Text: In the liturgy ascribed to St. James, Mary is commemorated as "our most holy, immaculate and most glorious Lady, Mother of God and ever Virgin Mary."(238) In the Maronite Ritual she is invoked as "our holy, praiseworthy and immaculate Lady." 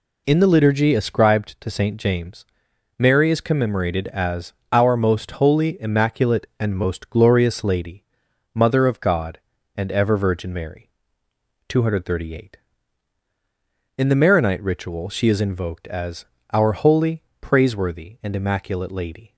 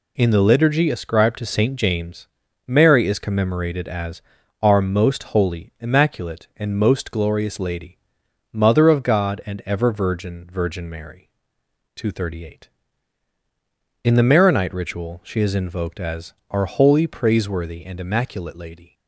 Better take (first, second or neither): first